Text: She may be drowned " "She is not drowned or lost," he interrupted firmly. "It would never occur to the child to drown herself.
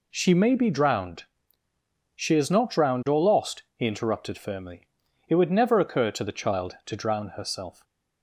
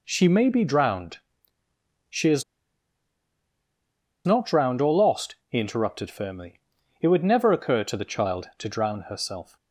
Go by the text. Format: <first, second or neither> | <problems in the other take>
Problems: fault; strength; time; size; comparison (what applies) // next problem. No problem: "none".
first | pauses between "is" and "not"; strong; at 2.4 s; 1.8 s long